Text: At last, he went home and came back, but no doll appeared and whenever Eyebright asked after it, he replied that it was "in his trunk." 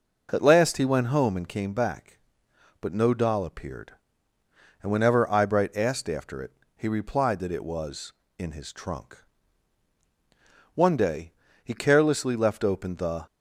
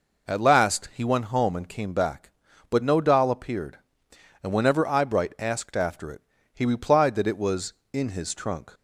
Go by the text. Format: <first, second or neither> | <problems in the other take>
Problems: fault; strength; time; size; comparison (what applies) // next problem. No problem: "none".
second | goes on to say "One day he carelessly left open the"; strong; from 10.7 s on; 2.5 s long